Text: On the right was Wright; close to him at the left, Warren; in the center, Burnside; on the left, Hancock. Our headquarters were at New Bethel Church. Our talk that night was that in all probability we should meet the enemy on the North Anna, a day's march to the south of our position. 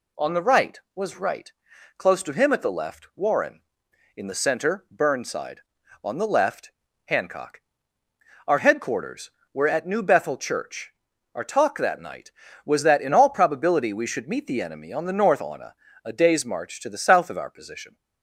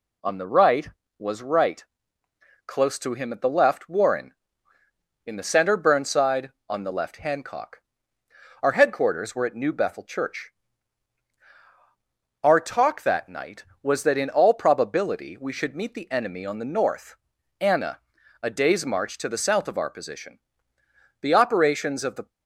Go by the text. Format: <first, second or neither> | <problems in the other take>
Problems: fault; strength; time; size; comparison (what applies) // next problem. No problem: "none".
first | pauses between "North" and "Anna"; noticeable; at 17.1 s; 0.46 s long // goes on to say "The operations of the"; noticeable; from 21.2 s on; 1.0 s long